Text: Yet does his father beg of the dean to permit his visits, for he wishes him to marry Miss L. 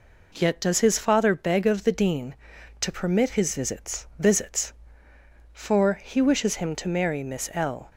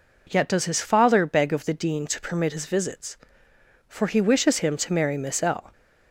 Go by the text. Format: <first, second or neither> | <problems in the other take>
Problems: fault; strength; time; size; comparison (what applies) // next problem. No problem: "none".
second | says "visits" twice; at 4.1 s